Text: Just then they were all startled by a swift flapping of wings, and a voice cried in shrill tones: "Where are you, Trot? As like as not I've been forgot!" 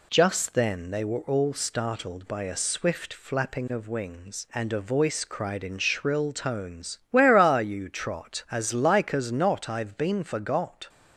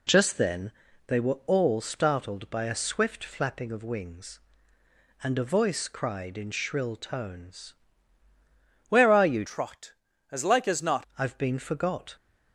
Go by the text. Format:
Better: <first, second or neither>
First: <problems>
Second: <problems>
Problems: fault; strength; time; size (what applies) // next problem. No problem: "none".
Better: first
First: none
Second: pauses between "then" and "they"; slight; at 0.7 s; 0.36 s long // changes voice from "Trot" to "not"; from 9.4 to 11.0 s; 1.6 s long